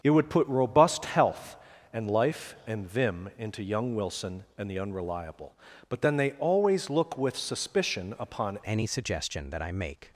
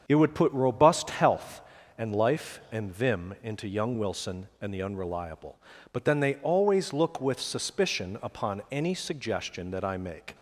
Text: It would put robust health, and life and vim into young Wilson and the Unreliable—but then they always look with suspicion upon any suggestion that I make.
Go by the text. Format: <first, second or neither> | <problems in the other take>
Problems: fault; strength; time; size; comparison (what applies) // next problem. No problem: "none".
second | starts louder than the rest; strong; until 1.0 s; 7 dB; strong in the second // changes voice at "any"; from 8.6 s on; 1.5 s long